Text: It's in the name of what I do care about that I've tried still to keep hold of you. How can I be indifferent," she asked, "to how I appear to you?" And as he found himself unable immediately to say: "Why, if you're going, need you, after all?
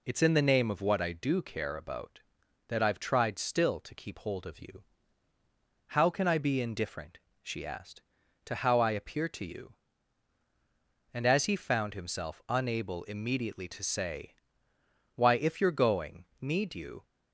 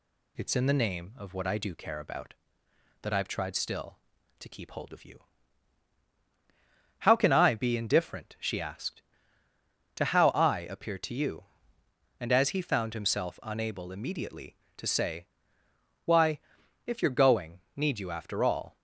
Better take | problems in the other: second | stops before "after all"; at 17.0 s

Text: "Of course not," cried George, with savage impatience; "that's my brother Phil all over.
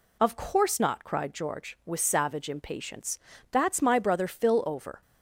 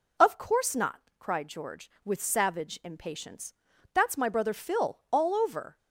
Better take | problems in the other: second | skips "all"; at 4.6 s

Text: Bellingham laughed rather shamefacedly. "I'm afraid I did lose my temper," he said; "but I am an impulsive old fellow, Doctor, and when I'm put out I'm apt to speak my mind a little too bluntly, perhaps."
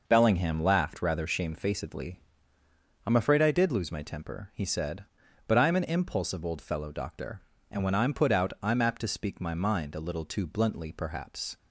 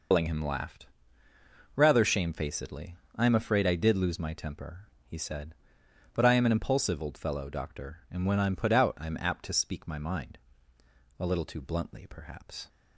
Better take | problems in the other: first | loses the start of "Bellingham"; at 0.1 s; 105 ms // pauses between "laughed" and "rather"; noticeable; at 0.8 s; 0.88 s long // pauses between "mind" and "a"; noticeable; at 10.3 s; 0.80 s long

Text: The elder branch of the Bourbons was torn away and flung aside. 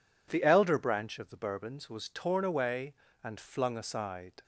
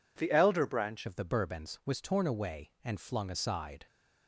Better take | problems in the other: first | changes voice at "of"; from 1.0 s on; 2.8 s long

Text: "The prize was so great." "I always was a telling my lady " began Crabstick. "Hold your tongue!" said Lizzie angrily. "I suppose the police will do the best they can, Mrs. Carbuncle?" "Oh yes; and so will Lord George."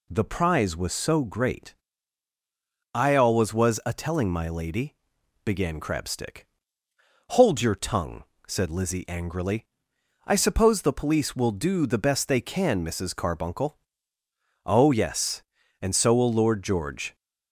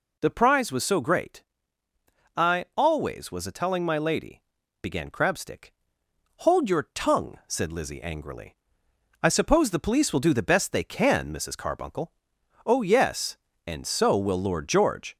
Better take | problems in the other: neither | none

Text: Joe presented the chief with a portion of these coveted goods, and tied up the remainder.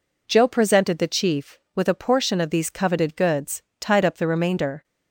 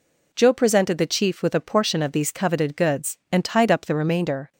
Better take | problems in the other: second | skips "and"; at 3.7 s

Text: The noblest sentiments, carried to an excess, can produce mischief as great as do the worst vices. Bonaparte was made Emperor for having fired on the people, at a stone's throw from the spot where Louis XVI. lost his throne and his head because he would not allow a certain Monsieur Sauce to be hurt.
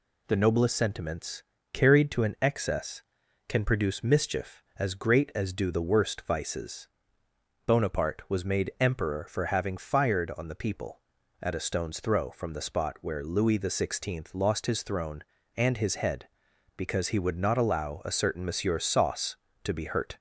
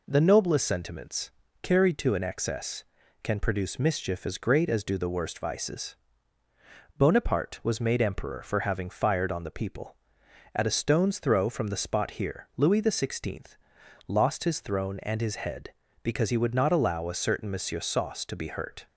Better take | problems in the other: first | says "here" for "where"; at 12.1 s

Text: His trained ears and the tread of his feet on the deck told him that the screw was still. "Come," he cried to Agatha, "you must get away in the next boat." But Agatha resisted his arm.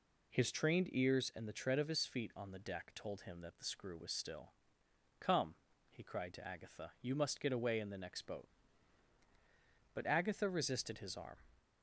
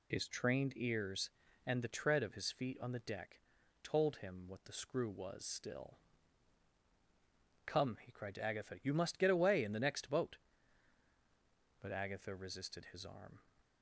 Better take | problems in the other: first | pauses between "deck" and "told"; at 3.3 s; 0.42 s long // says "what" for "that"; at 4.4 s

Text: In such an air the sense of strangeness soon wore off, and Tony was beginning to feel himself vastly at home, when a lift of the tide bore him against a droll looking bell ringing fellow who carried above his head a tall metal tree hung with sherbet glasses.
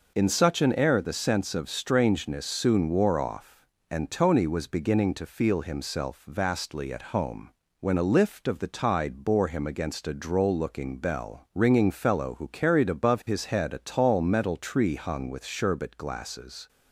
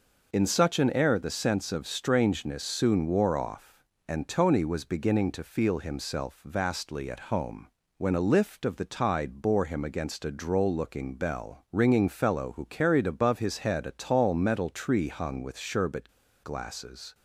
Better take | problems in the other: first | pauses between "sherbet" and "glasses"; slight; at 16.0 s; 0.34 s long

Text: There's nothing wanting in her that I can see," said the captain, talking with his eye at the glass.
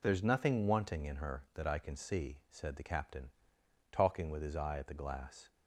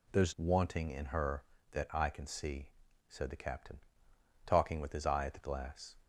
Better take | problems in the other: first | skips "nothing"; at 0.3 s

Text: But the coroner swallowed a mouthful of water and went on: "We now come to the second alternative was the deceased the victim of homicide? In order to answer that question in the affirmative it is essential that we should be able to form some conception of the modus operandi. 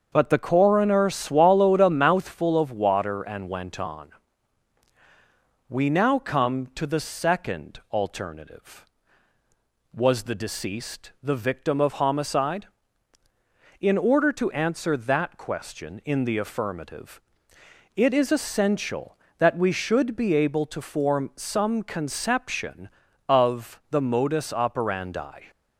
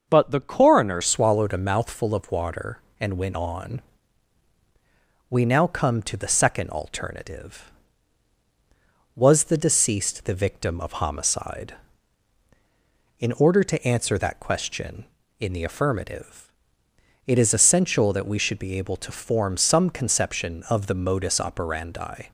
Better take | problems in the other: first | starts louder than the rest; until 1.0 s; 6 dB; also in the first // changes voice at "swallowed"; from 1.0 s on; 21.3 s long // pauses between "affirmative" and "it"; noticeable; at 16.4 s; 0.78 s long; noticeable in the first

